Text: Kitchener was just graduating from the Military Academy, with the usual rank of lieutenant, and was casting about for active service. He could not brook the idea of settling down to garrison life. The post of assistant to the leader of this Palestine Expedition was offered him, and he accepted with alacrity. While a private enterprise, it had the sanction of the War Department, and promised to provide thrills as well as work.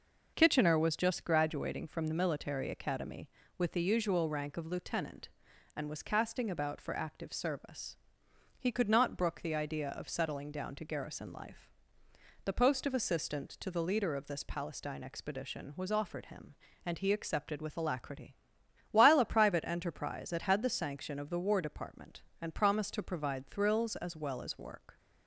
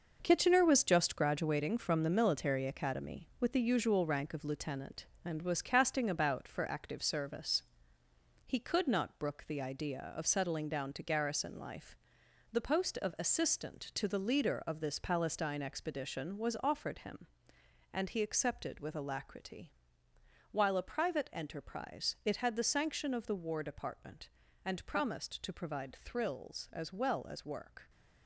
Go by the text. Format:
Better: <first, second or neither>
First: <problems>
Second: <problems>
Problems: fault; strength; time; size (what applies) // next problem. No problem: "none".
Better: first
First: none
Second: gets quieter; strong; throughout; 8 dB